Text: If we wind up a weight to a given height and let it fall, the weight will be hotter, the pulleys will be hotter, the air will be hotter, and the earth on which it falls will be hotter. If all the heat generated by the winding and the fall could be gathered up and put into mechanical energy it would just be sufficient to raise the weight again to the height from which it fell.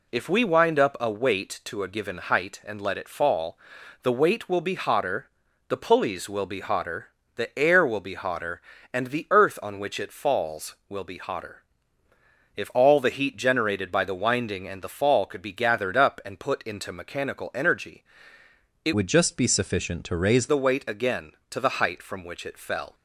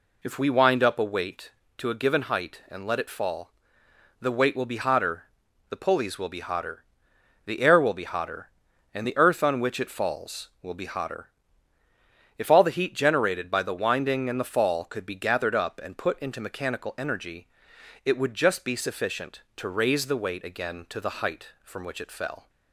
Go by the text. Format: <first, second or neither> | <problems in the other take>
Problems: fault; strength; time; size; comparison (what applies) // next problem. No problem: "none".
second | pauses between "energy" and "it"; noticeable; at 18.0 s; 0.82 s long; noticeable in the second // changes voice from "would" to "raise"; from 18.9 to 20.4 s; 1.5 s long